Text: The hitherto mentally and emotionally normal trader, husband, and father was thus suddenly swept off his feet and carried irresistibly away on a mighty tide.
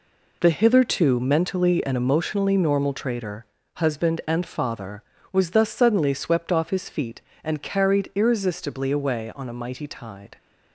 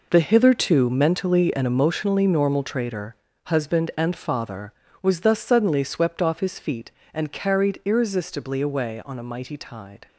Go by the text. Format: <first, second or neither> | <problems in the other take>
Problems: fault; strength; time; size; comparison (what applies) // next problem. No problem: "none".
first | gets quieter; strong; throughout; 11.5 dB